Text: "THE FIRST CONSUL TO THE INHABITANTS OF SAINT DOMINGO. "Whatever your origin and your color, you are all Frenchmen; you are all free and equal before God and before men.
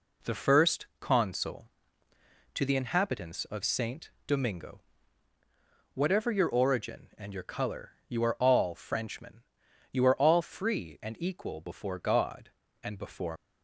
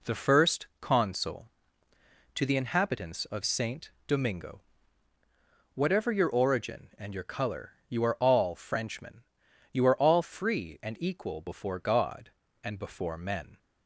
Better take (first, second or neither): second